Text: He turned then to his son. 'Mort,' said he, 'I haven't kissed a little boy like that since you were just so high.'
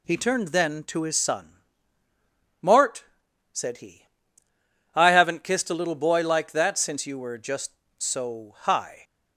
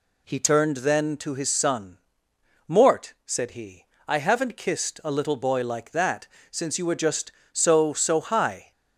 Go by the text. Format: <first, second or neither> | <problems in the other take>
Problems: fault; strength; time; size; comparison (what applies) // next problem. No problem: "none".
first | pauses between "that" and "since"; slight; at 6.2 s; 0.24 s long // says "so" twice; at 7.9 s